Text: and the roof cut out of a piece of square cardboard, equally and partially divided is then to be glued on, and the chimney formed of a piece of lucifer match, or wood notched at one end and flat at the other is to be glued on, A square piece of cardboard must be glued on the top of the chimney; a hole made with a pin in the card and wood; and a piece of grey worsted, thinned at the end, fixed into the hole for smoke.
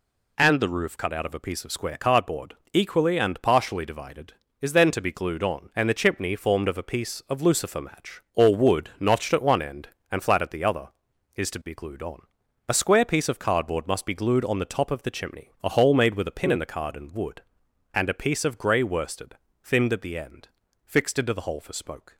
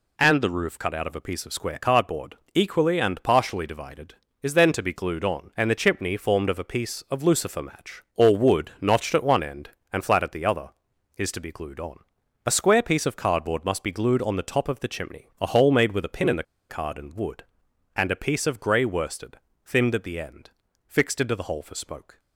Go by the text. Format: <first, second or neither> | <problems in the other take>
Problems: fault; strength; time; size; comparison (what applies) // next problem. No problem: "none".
first | pauses between "the" and "card"; slight; at 16.4 s; 0.27 s long